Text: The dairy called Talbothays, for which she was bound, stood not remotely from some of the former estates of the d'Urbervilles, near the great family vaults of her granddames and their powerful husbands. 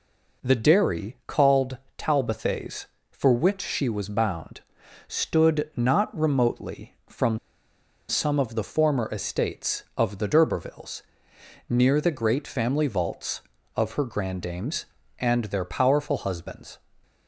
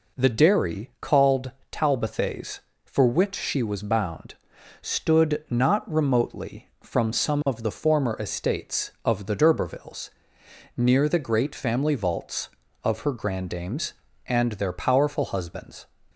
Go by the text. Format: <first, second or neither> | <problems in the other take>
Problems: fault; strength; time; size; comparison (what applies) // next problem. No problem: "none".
second | pauses between "called" and "Talbothays"; slight; at 1.7 s; 0.22 s long; slight in the second // pauses between "from" and "some"; noticeable; at 7.3 s; 0.70 s long